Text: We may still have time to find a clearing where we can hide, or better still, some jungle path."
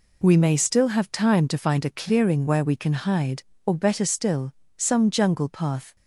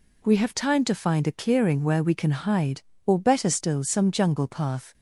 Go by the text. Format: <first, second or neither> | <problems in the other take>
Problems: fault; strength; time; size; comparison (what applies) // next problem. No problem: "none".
first | skips "may still"; at 0.3 s